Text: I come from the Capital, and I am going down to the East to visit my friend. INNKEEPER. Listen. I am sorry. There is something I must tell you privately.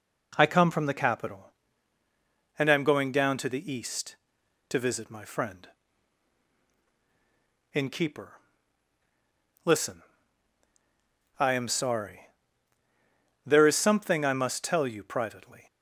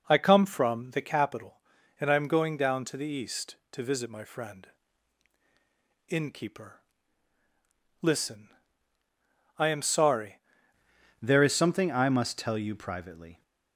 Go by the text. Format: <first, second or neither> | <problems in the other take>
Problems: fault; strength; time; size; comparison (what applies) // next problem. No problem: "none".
first | changes voice at "There"; from 11.2 s on; 2.2 s long